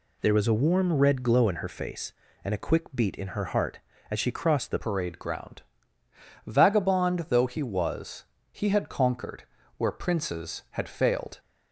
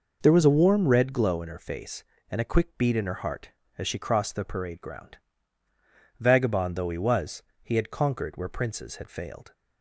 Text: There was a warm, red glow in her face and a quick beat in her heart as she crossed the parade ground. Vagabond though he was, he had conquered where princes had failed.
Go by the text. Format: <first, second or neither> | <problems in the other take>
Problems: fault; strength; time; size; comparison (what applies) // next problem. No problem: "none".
second | changes voice at "parade"; from 4.7 s on; 6.6 s long // pauses between "conquered" and "where"; slight; at 9.4 s; 0.34 s long